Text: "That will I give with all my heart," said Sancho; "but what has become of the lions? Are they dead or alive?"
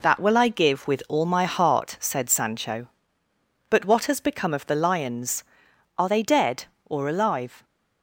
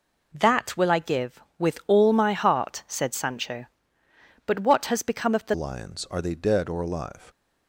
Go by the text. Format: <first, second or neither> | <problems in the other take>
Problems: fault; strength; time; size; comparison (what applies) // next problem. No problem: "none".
first | changes voice at "lions"; from 5.5 s on; 1.7 s long